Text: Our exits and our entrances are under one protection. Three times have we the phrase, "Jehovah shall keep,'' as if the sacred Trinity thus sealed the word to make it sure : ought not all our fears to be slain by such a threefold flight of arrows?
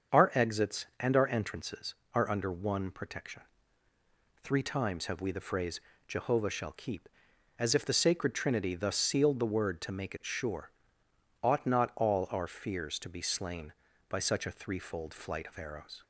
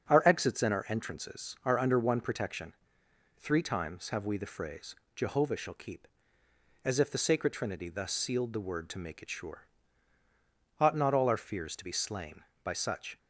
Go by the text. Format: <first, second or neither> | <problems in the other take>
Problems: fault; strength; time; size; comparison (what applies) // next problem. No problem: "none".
first | starts louder than the rest; strong; until 1.1 s; 7.5 dB; also in the first // stops before "a threefold flight of arrows"; at 13.1 s